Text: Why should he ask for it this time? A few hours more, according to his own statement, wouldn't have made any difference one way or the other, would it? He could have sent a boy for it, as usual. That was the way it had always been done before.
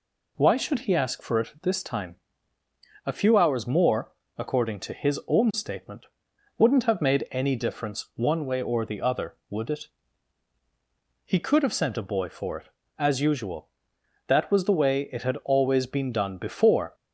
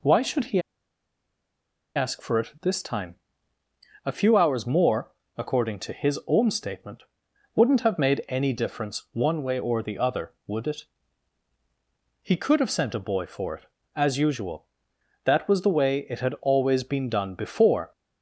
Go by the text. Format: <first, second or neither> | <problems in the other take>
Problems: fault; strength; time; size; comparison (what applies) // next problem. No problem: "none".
first | pauses between "he" and "ask"; strong; at 0.5 s; 1.3 s long